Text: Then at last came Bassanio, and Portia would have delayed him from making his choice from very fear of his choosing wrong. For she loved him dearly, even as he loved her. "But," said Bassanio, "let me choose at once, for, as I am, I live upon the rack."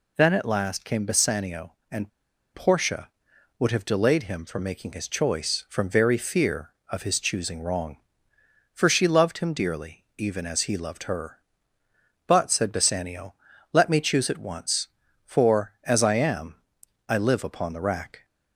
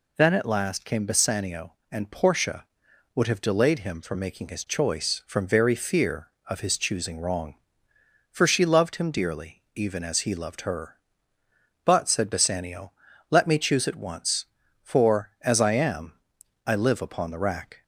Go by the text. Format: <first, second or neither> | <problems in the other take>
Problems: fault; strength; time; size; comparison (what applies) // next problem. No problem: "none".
second | pauses between "and" and "Portia"; at 2.0 s; 0.44 s long